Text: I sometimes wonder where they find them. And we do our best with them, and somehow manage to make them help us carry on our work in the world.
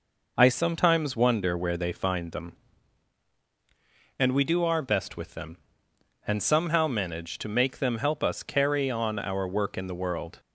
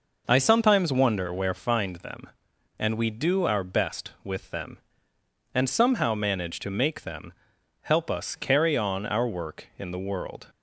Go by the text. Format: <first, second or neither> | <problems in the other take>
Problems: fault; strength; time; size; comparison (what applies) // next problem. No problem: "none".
first | skips "they"; at 1.5 s // pauses between "them" and "help"; noticeable; at 7.3 s; 0.50 s long